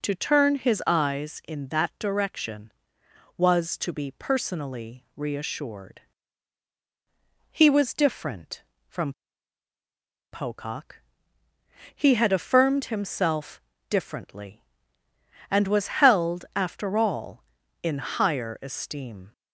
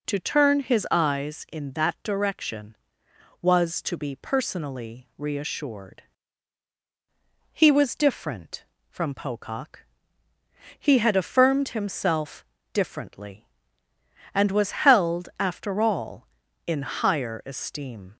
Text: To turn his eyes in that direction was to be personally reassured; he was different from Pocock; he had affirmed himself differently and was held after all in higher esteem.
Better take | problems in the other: second | pauses between "from" and "Pocock"; at 9.1 s; 1.1 s long // pauses between "himself" and "differently"; slight; at 13.6 s; 0.26 s long; slight in the second

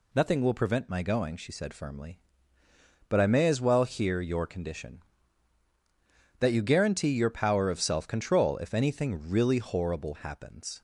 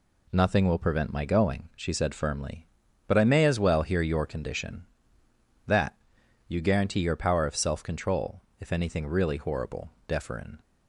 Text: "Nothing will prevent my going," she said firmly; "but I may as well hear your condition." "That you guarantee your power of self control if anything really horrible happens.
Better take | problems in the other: first | pauses between "That" and "you"; noticeable; at 5.9 s; 0.50 s long // pauses between "control" and "if"; slight; at 8.4 s; 0.18 s long // says "deferen" for "happens"; at 10.0 s

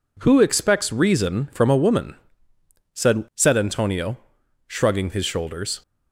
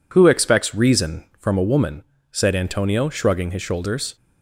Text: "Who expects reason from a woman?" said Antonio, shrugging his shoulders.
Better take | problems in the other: second | says "said" twice; at 3.3 s

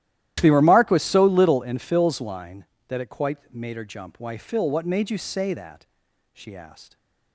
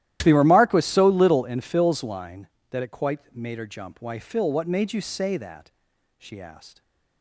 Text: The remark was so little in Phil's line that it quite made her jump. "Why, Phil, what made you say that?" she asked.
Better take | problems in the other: neither | starts louder than the rest; strong; the same in both

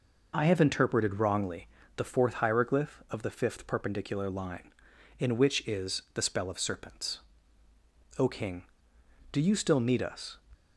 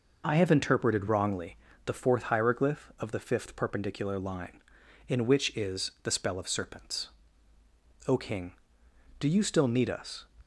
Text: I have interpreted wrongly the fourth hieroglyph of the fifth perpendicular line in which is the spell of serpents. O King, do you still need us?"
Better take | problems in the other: neither | pauses between "wrongly" and "the"; slight; the same in both

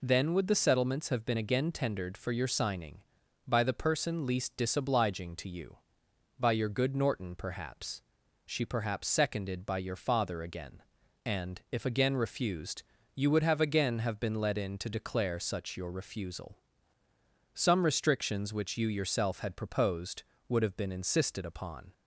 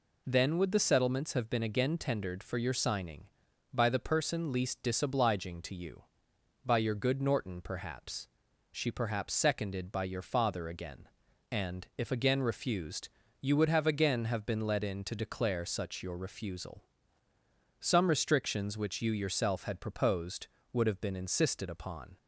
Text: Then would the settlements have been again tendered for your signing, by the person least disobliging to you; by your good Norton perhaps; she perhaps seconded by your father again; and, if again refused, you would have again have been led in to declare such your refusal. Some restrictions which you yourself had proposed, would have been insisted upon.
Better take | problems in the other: neither | none

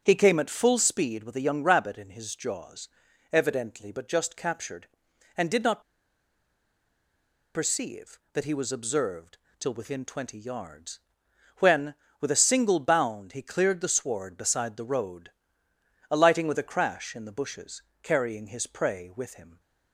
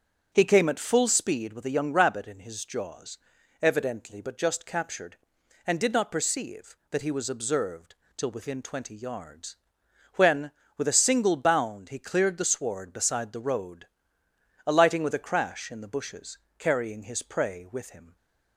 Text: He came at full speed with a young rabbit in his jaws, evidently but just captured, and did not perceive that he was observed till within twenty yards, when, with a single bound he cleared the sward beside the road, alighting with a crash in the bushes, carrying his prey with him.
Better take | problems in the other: second | starts louder than the rest; until 1.0 s; 6.5 dB; also in the second // pauses between "not" and "perceive"; strong; at 5.8 s; 1.7 s long // pauses between "observed" and "till"; slight; at 9.3 s; 0.22 s long; slight in the second

